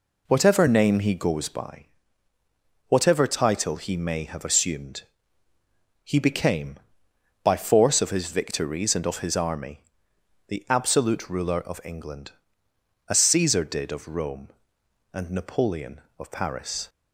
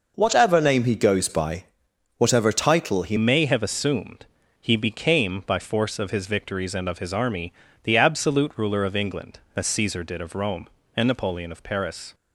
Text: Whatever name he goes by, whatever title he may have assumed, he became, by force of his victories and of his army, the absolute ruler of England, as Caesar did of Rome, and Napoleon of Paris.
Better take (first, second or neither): first